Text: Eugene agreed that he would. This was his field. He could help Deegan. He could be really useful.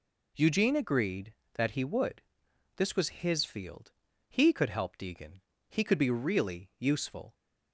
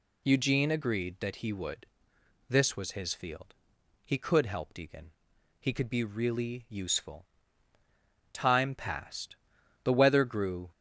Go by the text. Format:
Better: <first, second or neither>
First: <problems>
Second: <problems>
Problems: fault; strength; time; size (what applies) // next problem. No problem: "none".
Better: first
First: none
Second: goes on to say "Time passed The weather grew"; strong; from 8.3 s on; 2.3 s long